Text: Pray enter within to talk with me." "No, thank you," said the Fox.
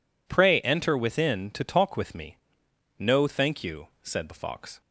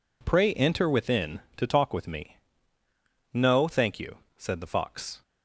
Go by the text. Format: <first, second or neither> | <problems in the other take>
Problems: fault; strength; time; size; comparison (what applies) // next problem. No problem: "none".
neither | none